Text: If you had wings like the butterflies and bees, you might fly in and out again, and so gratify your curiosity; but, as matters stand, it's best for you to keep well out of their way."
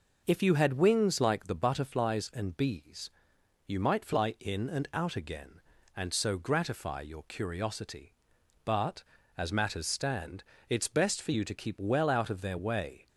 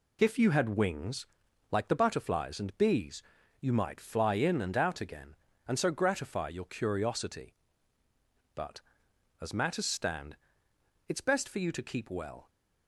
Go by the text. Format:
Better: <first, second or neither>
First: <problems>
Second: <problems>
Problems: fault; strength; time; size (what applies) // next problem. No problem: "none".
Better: first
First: none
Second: pauses between "wings" and "like"; noticeable; at 1.2 s; 0.46 s long // stops before "out of their way"; at 12.4 s